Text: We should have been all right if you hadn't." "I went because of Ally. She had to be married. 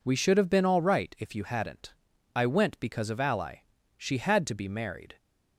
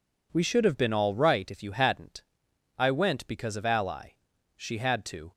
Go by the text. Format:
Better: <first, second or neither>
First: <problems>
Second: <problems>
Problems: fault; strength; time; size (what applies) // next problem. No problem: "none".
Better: first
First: none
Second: stops before "be married"; at 5.3 s